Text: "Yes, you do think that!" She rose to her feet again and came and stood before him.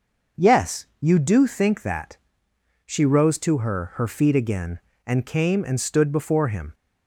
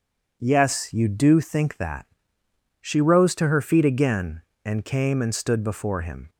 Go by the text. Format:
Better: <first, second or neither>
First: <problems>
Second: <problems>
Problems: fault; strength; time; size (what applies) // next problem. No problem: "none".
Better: second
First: says "her" twice; at 3.9 s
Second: none